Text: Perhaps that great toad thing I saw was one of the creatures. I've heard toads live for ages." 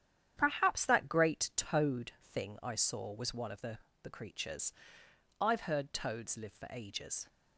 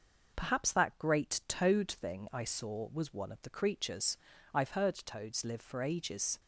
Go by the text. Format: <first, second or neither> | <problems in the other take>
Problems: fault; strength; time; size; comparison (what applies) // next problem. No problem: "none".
second | starts louder than the rest; strong; until 1.3 s; 9.5 dB // says "the" twice; at 4.0 s